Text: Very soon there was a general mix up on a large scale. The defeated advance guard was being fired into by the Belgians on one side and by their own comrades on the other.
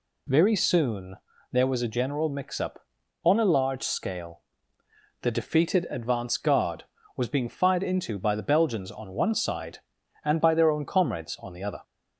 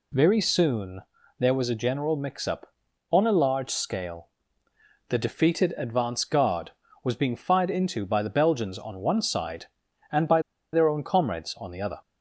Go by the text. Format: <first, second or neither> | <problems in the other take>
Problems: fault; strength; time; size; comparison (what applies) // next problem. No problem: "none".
first | pauses between "soon" and "there"; at 1.0 s; 0.38 s long; slight in the first // pauses between "by" and "their"; slight; at 10.4 s; 0.31 s long